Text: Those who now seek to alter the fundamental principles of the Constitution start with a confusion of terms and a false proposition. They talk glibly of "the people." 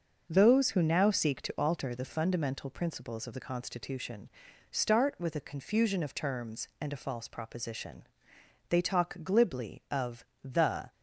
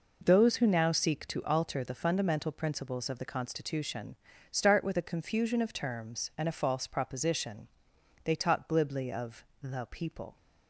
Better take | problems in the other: second | pauses between "Constitution" and "start"; at 4.2 s; 0.42 s long; also in the second // pauses between "of" and "the"; slight; at 10.2 s; 0.20 s long; slight in the second // stops before "people"; at 10.9 s

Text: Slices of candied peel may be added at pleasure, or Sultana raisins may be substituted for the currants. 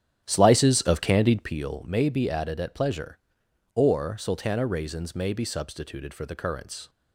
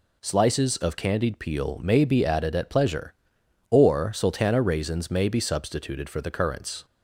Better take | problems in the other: second | starts louder than the rest; strong; until 1.6 s; 10 dB

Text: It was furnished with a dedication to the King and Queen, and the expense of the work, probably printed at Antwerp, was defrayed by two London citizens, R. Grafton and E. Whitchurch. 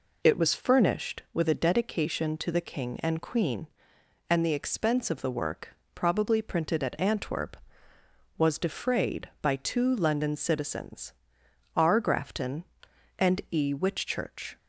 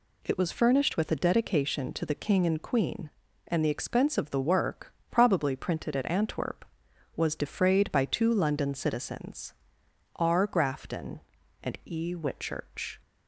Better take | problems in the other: neither | none

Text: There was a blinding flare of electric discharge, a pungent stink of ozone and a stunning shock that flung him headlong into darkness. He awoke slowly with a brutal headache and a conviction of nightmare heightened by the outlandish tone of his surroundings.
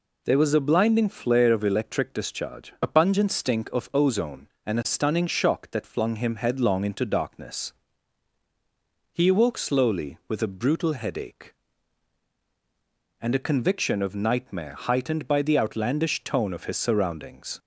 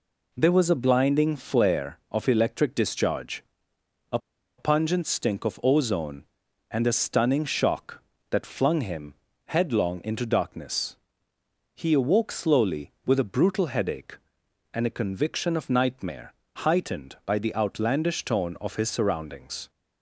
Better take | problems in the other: first | pauses between "a" and "pungent"; at 4.1 s; 0.39 s long // pauses between "him" and "headlong"; slight; at 9.1 s; 0.32 s long // pauses between "nightmare" and "heightened"; slight; at 16.3 s; 0.24 s long

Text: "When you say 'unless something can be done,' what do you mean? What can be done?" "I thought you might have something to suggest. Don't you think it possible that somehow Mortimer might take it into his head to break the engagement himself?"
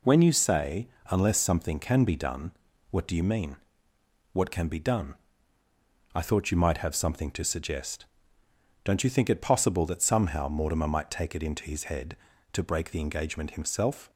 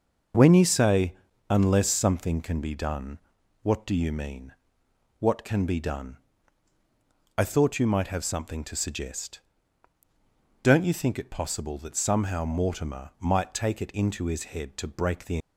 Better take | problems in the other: first | starts louder than the rest; noticeable; until 1.7 s; 6 dB // pauses between "say" and "unless"; slight; at 1.1 s; 0.34 s long; slight in the first // stops before "engagement himself"; at 15.3 s

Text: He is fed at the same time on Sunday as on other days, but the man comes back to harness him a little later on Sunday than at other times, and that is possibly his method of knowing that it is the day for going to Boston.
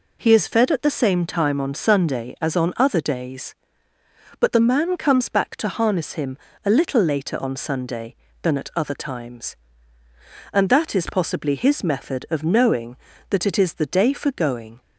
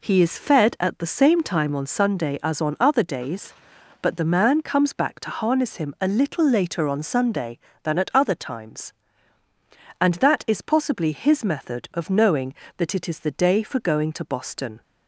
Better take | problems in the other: second | pauses between "him" and "a"; slight; at 6.3 s; 0.26 s long // stops before "to Boston"; at 14.8 s

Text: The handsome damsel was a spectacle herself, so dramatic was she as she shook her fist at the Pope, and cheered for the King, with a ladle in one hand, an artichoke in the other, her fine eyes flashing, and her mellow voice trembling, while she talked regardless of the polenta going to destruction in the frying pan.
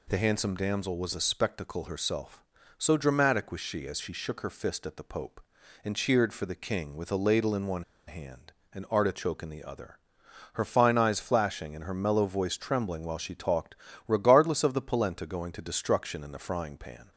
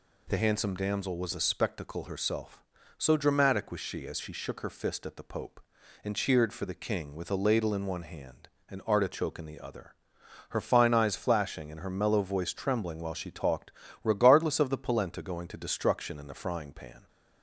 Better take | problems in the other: second | pauses between "one" and "hand"; slight; at 7.8 s; 0.24 s long // pauses between "talked" and "regardless"; slight; at 13.7 s; 0.32 s long; slight in the second

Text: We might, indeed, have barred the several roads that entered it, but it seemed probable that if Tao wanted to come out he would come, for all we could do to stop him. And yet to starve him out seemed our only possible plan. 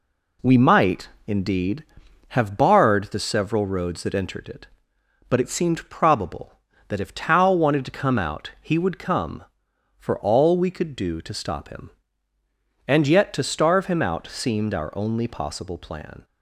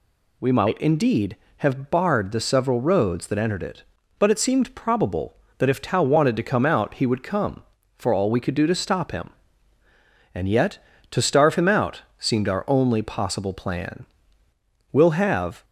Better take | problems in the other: first | pauses between "out" and "seemed"; slight; at 12.0 s; 0.16 s long // goes on to say "We'll have"; noticeable; from 14.9 s on; 0.72 s long

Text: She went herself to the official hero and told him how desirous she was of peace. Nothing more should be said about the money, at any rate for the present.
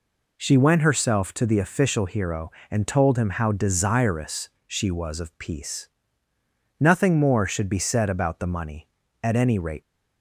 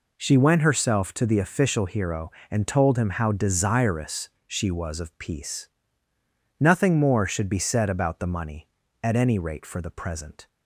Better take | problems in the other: second | pauses between "desirous" and "she"; slight; at 4.4 s; 0.16 s long; slight in the second // stops before "for the present"; at 9.8 s

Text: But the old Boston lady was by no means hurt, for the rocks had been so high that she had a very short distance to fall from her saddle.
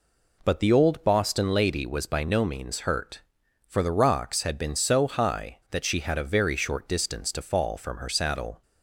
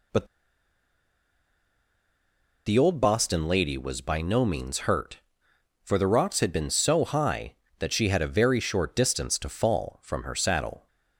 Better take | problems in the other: first | pauses between "But" and "the"; strong; at 0.2 s; 2.4 s long

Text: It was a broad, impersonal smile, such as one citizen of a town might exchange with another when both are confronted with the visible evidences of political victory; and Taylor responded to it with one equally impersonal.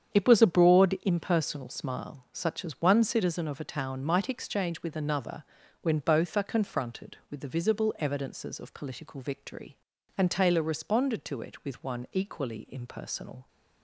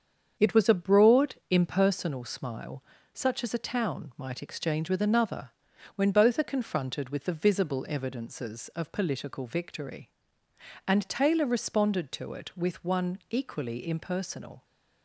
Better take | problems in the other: first | starts louder than the rest; strong; until 1.5 s; 7.5 dB; strong in the first // skips "one citizen of"; at 3.5 s // pauses between "another" and "when"; at 5.4 s; 0.44 s long; also in the first

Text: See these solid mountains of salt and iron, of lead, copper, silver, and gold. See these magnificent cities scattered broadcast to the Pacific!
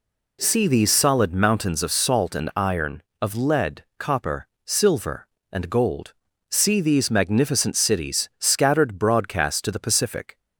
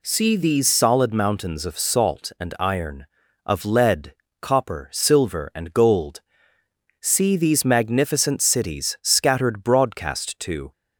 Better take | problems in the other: first | stops before "the Pacific"; at 10.7 s

